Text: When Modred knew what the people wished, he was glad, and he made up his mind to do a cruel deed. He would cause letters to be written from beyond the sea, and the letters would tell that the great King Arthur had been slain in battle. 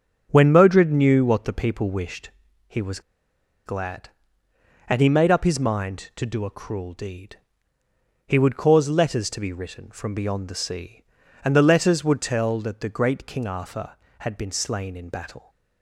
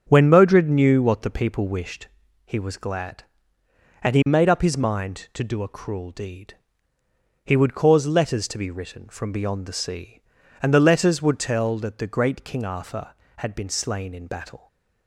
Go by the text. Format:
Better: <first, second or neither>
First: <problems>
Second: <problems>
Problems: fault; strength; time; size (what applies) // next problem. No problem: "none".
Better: second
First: starts louder than the rest; strong; until 1.3 s; 7.5 dB // pauses between "was" and "glad"; noticeable; at 3.0 s; 0.65 s long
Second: starts louder than the rest; strong; until 1.1 s; 7.5 dB